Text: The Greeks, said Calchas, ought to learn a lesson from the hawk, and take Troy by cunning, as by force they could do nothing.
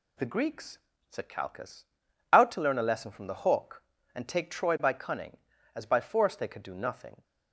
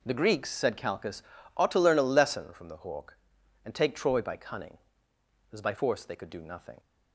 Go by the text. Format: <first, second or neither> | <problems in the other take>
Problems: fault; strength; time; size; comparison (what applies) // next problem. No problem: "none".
second | says "out" for "ought"; at 2.3 s